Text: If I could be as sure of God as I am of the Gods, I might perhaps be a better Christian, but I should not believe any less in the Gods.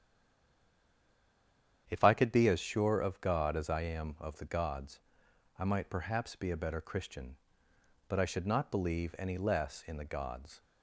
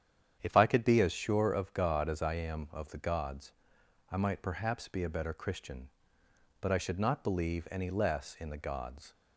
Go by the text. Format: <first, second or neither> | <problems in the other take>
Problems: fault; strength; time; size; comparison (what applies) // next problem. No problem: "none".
second | stays silent before the first word; noticeable; until 1.8 s; 1.8 s long // starts louder than the rest; strong; until 2.8 s; 9 dB; strong in the second